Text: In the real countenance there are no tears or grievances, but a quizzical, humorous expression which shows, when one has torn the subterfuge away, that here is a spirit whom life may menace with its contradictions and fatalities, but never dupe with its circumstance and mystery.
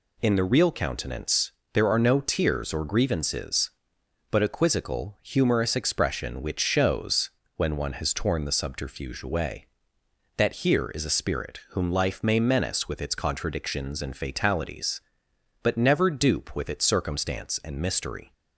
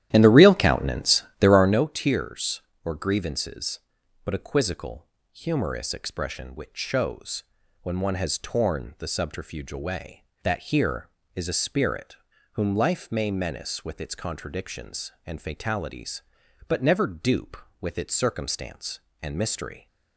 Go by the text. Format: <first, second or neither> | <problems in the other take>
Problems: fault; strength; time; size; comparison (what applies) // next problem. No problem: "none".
first | starts louder than the rest; strong; until 1.8 s; 12 dB // pauses between "countenance" and "there"; slight; at 1.2 s; 0.16 s long; slight in the first // pauses between "spirit" and "whom"; at 12.1 s; 0.38 s long